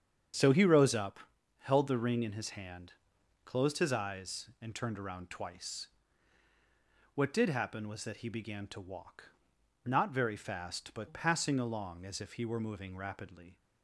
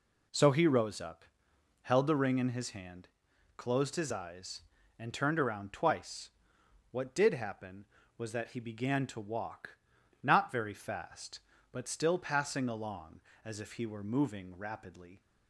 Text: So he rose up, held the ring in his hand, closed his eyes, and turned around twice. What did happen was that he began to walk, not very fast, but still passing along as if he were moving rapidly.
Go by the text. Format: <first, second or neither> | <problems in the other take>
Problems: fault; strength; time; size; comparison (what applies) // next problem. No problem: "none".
second | starts louder than the rest; strong; until 1.7 s; 8 dB // skips "still"; at 11.0 s